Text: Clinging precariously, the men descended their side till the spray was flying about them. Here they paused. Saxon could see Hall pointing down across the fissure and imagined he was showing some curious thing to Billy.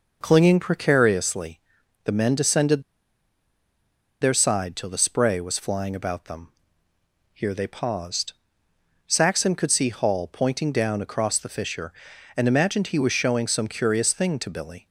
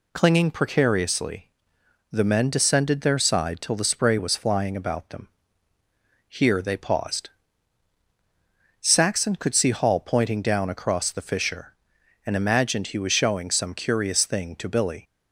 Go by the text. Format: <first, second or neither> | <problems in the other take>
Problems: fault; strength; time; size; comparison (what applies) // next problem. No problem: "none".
second | pauses between "descended" and "their"; strong; at 2.8 s; 1.3 s long